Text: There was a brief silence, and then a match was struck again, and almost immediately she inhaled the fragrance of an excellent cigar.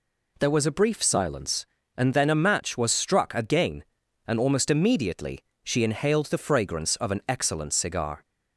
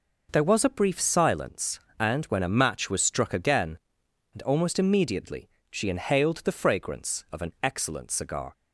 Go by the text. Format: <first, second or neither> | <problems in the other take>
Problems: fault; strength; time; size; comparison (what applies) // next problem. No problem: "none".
first | says "when" for "then"; at 2.2 s // pauses between "immediately" and "she"; slight; at 5.4 s; 0.22 s long; slight in the first